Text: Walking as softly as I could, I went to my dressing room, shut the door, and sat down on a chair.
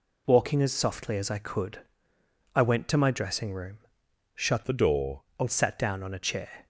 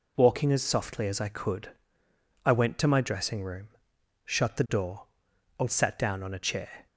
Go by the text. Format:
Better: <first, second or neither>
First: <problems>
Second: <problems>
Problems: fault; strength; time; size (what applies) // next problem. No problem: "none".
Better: second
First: changes voice from "the" to "door"; from 4.6 to 5.2 s; 0.6 s long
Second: none